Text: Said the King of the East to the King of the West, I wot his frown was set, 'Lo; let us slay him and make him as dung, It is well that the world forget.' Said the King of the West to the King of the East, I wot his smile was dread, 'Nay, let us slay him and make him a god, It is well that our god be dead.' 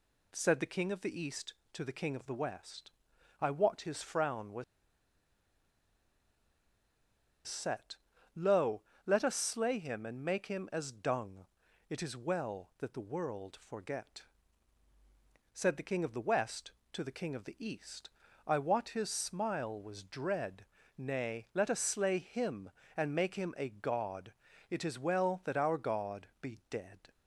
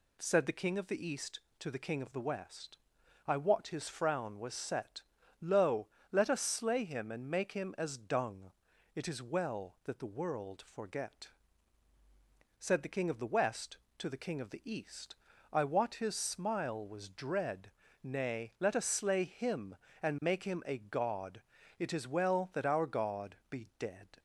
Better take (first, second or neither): second